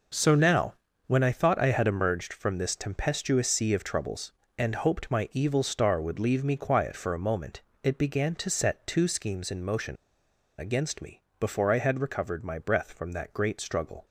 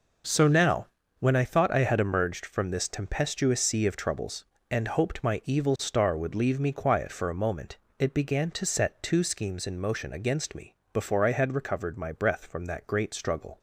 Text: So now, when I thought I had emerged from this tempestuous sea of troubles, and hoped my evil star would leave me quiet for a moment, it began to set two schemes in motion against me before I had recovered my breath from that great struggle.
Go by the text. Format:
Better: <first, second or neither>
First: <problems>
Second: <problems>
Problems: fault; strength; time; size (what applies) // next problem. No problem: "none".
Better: second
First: pauses between "motion" and "against"; noticeable; at 9.9 s; 0.63 s long // pauses between "me" and "before"; slight; at 11.2 s; 0.18 s long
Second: pauses between "me" and "before"; slight; at 10.7 s; 0.18 s long